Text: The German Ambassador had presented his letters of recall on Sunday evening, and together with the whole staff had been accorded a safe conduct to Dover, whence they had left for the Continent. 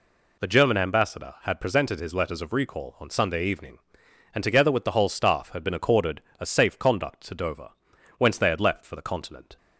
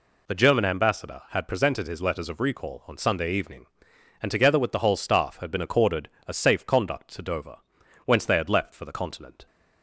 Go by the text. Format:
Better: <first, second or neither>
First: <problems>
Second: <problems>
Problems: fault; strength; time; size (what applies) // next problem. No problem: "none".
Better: neither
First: pauses between "accorded" and "a"; slight; at 6.1 s; 0.20 s long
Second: pauses between "accorded" and "a"; slight; at 6.0 s; 0.20 s long